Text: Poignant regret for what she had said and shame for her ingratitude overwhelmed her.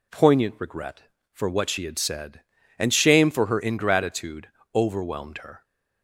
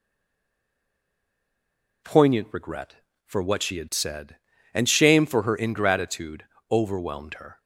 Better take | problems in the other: first | stays silent before the first word; noticeable; until 2.0 s; 2.0 s long // pauses between "ingratitude" and "overwhelmed"; slight; at 6.4 s; 0.26 s long; slight in the first

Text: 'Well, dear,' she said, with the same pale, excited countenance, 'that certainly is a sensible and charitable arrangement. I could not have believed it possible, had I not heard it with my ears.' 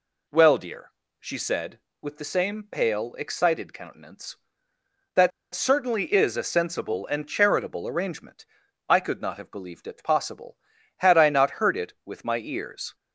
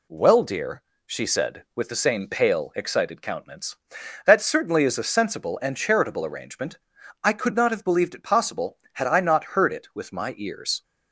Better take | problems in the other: second | pauses between "that" and "certainly"; slight; at 5.3 s; 0.24 s long

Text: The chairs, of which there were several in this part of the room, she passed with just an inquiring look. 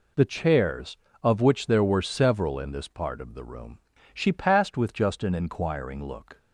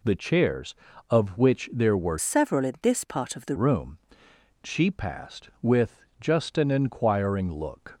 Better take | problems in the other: first | changes voice from "several" to "the"; from 2.1 to 3.5 s; 1.4 s long // pauses between "with" and "just"; slight; at 6.0 s; 0.18 s long

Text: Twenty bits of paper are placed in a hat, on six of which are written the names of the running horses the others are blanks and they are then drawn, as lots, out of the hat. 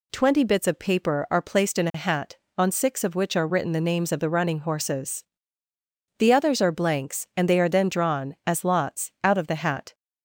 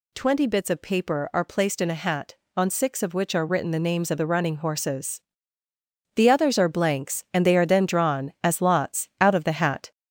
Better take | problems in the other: first | gets louder; noticeable; throughout; 4.5 dB // pauses between "horses" and "the"; noticeable; at 5.2 s; 0.96 s long; noticeable in the first

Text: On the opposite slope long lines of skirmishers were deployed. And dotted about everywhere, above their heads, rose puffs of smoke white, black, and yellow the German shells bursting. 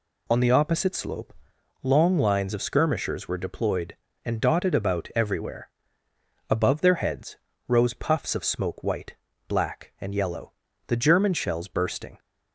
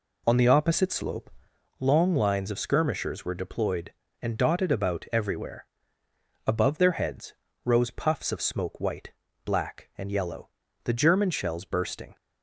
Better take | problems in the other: first | starts louder than the rest; until 1.9 s; 3.5 dB // pauses between "slope" and "long"; noticeable; at 1.2 s; 0.50 s long; noticeable in the first // pauses between "yellow" and "the"; at 10.4 s; 0.38 s long; also in the first

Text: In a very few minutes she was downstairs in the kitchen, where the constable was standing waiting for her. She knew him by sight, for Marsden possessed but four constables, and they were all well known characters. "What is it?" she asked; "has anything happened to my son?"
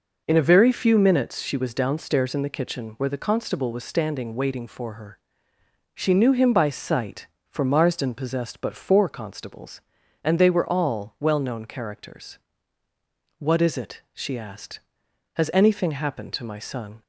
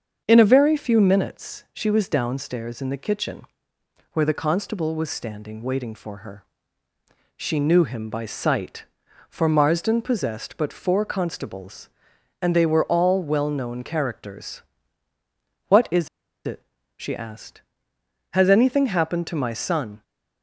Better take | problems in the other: first | starts louder than the rest; until 1.2 s; 7 dB // pauses between "is" and "it"; at 16.0 s; 0.38 s long

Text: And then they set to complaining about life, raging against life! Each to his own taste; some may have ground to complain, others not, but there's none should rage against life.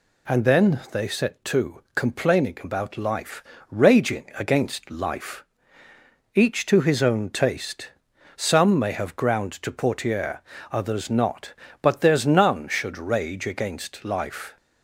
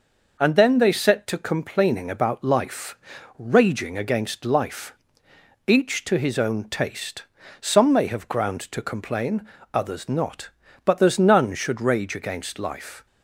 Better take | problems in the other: second | says "portiere" for "complain"; at 9.7 s

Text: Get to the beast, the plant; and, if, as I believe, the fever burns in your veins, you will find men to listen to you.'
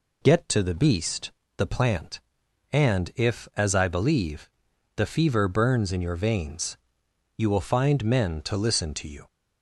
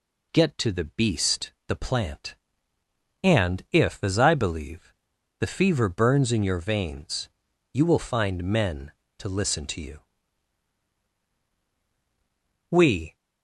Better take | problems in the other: first | goes on to say "We"; slight; from 12.6 s on; 0.46 s long

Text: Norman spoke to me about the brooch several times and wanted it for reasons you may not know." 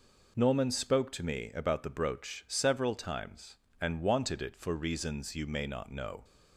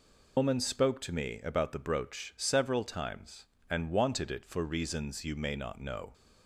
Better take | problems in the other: first | loses the start of "Norman"; at 0.3 s; 120 ms

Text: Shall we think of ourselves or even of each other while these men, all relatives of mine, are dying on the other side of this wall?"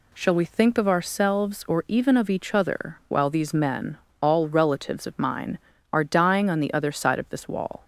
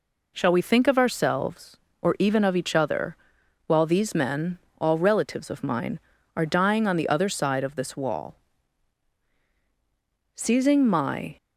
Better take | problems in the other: first | pauses between "other" and "while"; noticeable; at 3.1 s; 0.52 s long // goes on to say "Seizing my"; noticeable; from 10.3 s on; 1.0 s long

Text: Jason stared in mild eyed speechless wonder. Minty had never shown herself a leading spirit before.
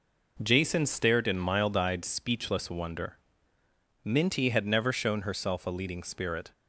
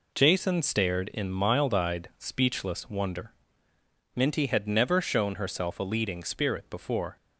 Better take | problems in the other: second | stops before "before"; at 6.5 s

